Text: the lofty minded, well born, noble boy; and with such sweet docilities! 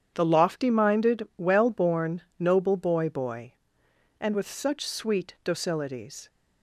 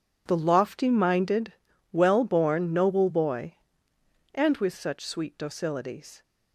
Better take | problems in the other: second | starts louder than the rest; strong; until 1.1 s; 8.5 dB // says "boy" twice; at 3.0 s

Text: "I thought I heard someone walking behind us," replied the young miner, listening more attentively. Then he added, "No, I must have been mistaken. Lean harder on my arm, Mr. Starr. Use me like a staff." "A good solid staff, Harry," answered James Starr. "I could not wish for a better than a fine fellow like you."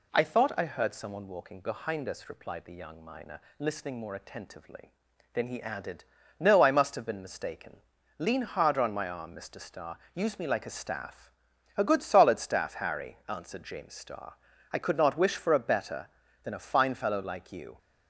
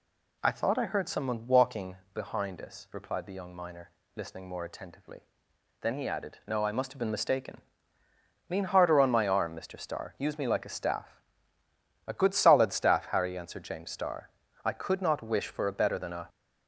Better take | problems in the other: first | pauses between "walking" and "behind"; slight; at 1.9 s; 0.18 s long // stops before "fine fellow like you"; at 16.2 s

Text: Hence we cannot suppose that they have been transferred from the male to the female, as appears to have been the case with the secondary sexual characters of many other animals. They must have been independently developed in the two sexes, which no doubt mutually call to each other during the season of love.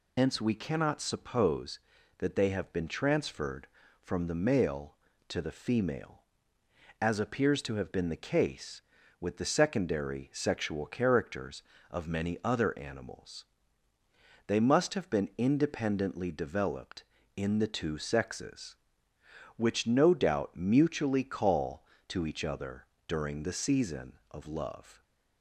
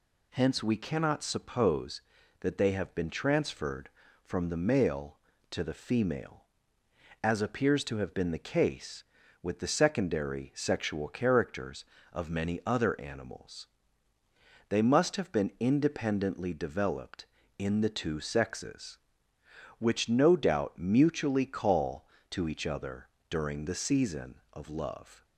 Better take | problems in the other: second | loses the start of "Hence"; at 0.1 s; 85 ms // pauses between "other" and "during"; slight; at 22.8 s; 0.20 s long; slight in the second

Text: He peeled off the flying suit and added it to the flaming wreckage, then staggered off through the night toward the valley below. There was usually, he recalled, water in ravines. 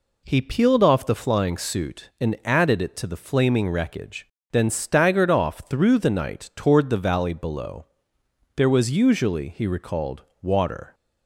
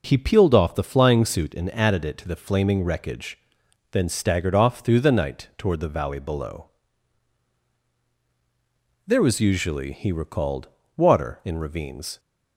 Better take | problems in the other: second | stops before "in ravines"; at 10.9 s

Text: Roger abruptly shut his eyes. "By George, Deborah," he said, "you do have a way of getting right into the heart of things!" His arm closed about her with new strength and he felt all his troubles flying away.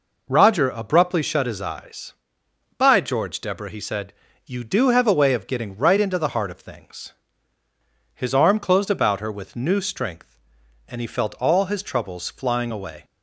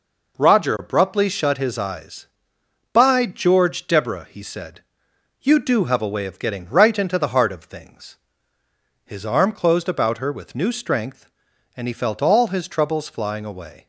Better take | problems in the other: neither | none

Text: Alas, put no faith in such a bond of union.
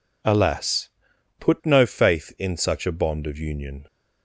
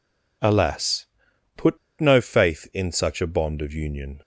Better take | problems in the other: first | pauses between "put" and "no"; slight; at 1.7 s; 0.22 s long

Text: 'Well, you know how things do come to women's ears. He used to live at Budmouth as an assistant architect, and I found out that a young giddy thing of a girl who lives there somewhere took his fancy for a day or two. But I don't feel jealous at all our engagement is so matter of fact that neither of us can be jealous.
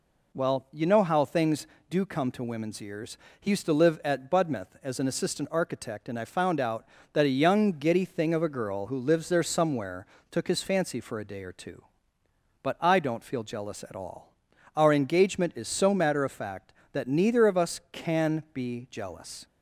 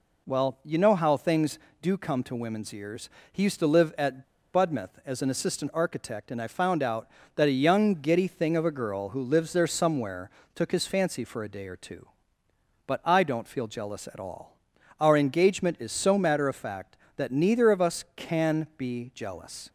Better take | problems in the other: first | pauses between "at" and "Budmouth"; slight; at 4.2 s; 0.30 s long // pauses between "somewhere" and "took"; slight; at 10.2 s; 0.24 s long; slight in the first // pauses between "all" and "our"; noticeable; at 14.5 s; 0.48 s long; noticeable in the first

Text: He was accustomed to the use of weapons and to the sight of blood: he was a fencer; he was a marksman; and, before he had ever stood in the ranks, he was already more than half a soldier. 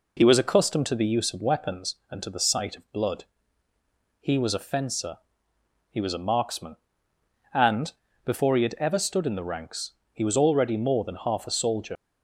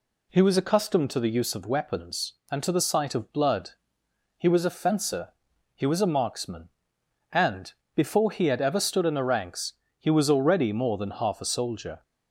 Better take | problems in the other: second | leaves "soldier" unfinished; at 11.9 s; 45 ms

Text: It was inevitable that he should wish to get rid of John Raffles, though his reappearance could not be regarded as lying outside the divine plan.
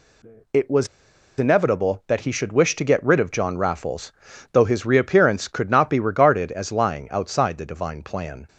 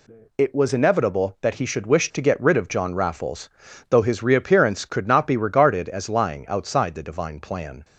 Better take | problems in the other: second | pauses between "was" and "inevitable"; noticeable; at 0.8 s; 0.51 s long

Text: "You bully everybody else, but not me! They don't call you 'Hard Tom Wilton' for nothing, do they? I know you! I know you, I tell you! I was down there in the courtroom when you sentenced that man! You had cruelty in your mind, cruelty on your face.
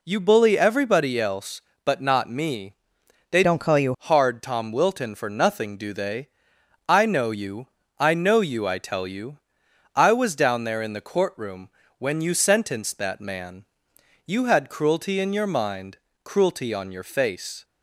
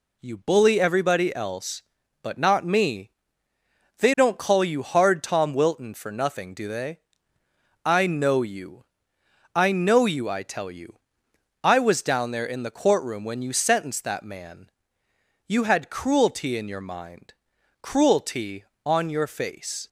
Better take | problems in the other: second | changes voice from "don't" to "you"; from 3.4 to 3.9 s; 0.5 s long // pauses between "courtroom" and "when"; slight; at 11.7 s; 0.26 s long

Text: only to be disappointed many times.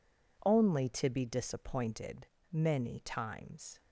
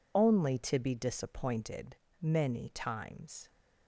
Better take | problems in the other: first | loses the start of "only"; at 0.1 s; 55 ms // pauses between "disappointed" and "many"; slight; at 1.9 s; 0.26 s long; slight in the first

